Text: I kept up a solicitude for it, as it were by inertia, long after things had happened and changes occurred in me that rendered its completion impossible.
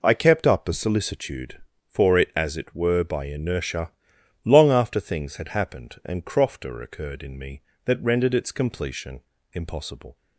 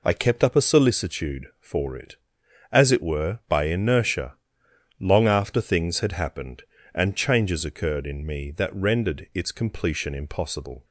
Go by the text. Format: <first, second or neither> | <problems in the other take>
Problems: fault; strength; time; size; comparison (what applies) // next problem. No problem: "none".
second | says "crofter" for "changes"; at 6.2 s // pauses between "completion" and "impossible"; slight; at 9.2 s; 0.32 s long